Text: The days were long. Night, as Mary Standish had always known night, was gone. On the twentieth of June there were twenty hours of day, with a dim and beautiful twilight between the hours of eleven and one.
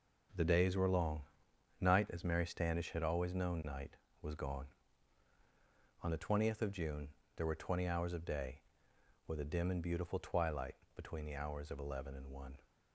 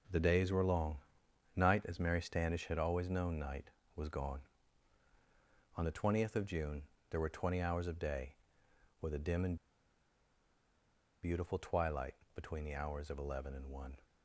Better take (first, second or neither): first